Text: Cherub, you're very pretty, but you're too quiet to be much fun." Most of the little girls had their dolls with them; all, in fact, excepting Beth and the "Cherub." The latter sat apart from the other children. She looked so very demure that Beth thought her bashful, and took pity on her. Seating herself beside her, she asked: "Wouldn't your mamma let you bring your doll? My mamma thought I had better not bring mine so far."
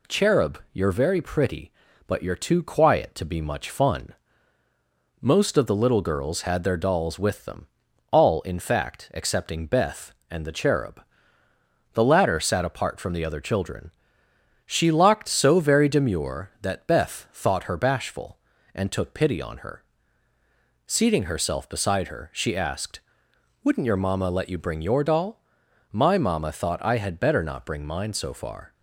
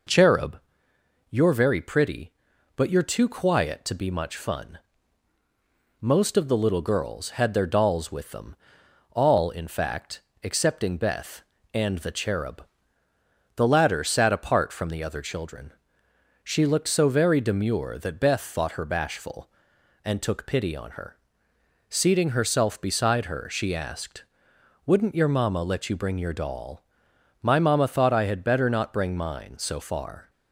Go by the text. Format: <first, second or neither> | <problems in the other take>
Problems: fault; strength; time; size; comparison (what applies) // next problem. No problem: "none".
second | says "locked" for "looked"; at 14.9 s